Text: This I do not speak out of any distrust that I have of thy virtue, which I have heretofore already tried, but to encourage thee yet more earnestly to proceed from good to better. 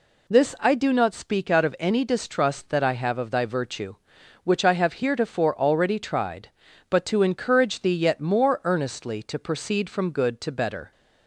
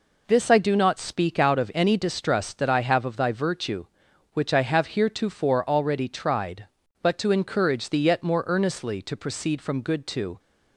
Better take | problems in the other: first | stops before "better"; at 10.3 s

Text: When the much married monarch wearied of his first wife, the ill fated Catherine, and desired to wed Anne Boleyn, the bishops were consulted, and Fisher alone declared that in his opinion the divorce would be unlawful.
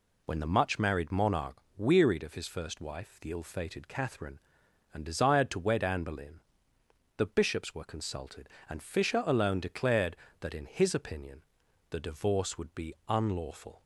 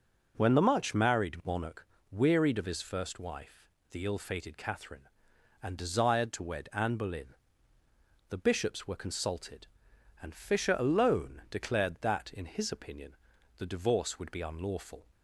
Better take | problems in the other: neither | pauses between "monarch" and "wearied"; slight; the same in both // pauses between "opinion" and "the"; the same in both

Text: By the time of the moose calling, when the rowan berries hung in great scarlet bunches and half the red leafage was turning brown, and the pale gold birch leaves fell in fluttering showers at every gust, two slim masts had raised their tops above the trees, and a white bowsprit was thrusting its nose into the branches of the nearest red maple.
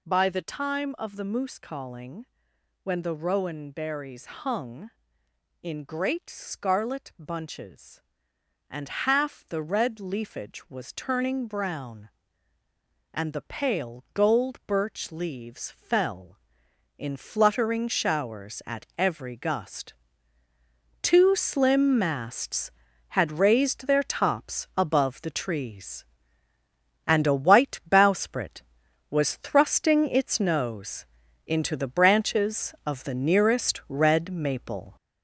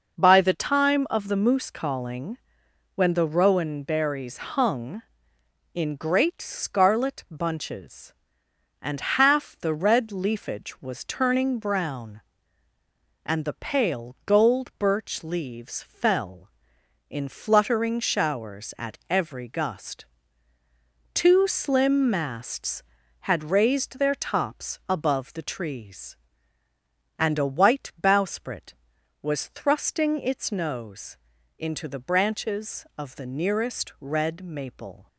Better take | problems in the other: second | gets louder; noticeable; throughout; 6 dB // pauses between "nose" and "into"; at 31.0 s; 0.40 s long; also in the second

